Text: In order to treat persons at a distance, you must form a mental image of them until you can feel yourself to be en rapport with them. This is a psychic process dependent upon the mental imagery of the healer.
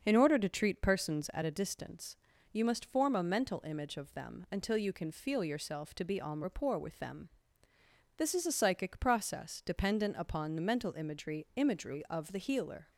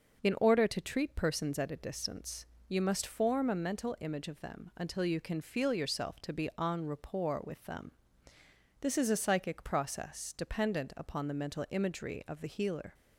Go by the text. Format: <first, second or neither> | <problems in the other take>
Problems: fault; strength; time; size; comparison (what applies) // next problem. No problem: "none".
second | starts louder than the rest; until 1.0 s; 6.5 dB // says "imagery" twice; at 11.5 s